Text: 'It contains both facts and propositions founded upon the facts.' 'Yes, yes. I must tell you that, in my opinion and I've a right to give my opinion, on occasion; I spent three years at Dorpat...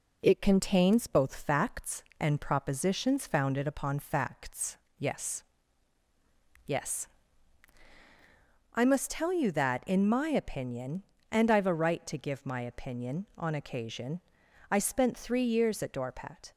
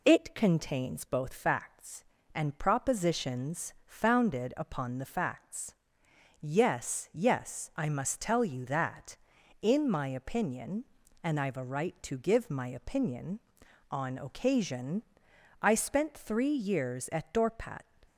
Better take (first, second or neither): second